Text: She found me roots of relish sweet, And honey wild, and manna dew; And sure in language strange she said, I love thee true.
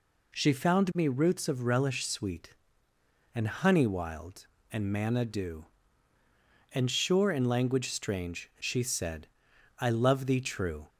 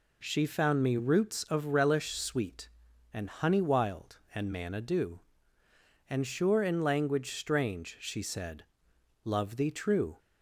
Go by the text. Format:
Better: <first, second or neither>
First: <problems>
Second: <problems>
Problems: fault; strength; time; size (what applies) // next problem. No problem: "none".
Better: first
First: none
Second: skips "I"; at 8.9 s